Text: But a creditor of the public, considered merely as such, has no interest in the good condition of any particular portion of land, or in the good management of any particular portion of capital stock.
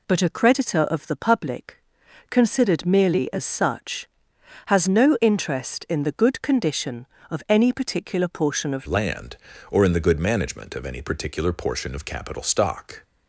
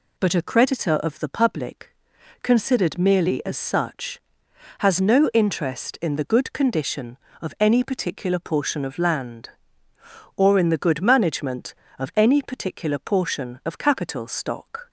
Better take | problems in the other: second | changes voice at "land"; from 8.8 s on; 4.2 s long

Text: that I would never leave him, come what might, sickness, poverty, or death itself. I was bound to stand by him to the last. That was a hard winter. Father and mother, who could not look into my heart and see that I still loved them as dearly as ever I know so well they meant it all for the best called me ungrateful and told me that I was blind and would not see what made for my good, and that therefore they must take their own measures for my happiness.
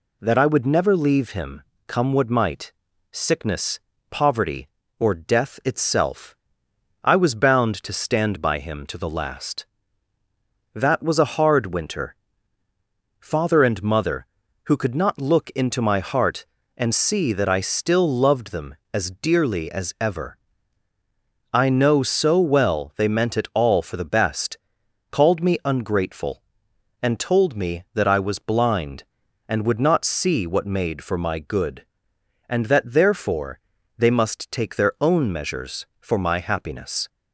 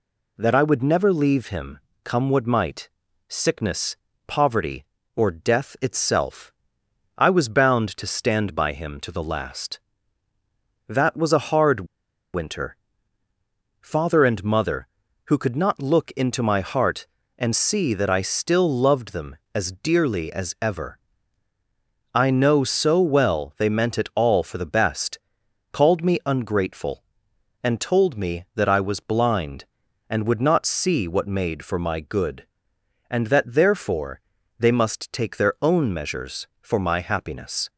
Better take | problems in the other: first | pauses between "hard" and "winter"; noticeable; at 11.8 s; 0.48 s long // pauses between "ever" and "I"; at 20.9 s; 1.1 s long; also in the first // pauses between "best" and "called"; noticeable; at 25.1 s; 0.54 s long; noticeable in the first // pauses between "therefore" and "they"; slight; at 34.2 s; 0.36 s long; slight in the first

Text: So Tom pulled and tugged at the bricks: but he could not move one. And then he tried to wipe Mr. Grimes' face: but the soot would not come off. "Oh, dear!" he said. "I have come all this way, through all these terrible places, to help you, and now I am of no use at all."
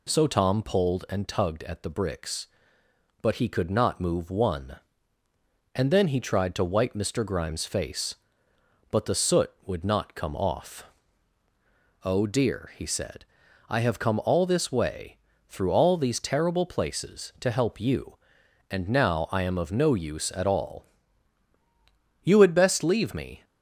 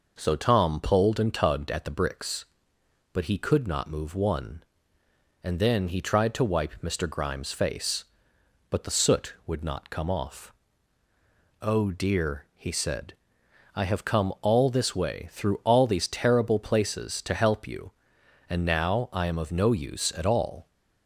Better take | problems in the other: second | goes on to say "You had best leave me"; noticeable; from 22.2 s on; 1.2 s long

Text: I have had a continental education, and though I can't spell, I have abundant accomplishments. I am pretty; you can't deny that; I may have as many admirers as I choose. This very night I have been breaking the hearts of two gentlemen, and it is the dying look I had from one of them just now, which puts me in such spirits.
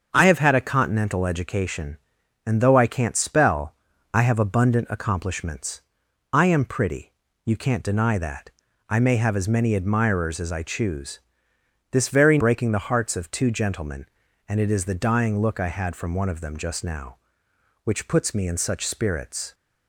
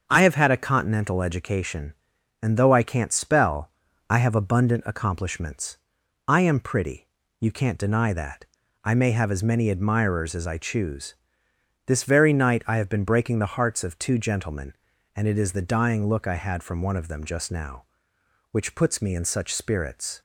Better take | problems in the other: second | starts louder than the rest; until 1.1 s; 7 dB; also in the second // skips "night I have been"; at 12.3 s

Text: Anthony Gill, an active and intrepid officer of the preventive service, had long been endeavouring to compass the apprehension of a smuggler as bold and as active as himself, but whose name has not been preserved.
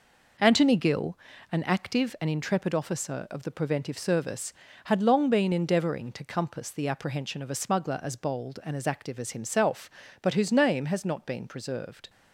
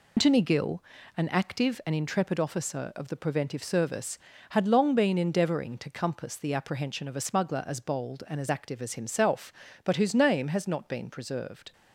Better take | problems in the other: first | loses the start of "Anthony"; at 0.1 s; 125 ms

